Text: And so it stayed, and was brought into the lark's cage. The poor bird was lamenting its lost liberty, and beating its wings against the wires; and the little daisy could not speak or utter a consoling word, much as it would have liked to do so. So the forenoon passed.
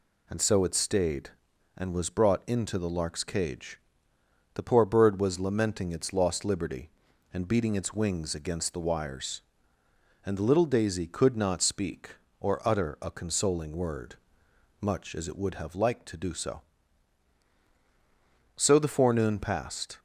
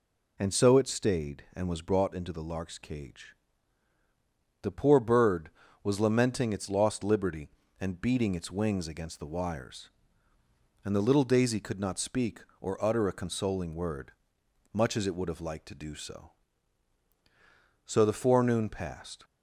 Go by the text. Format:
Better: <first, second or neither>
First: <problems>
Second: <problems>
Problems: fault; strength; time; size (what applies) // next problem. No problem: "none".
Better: neither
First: none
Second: none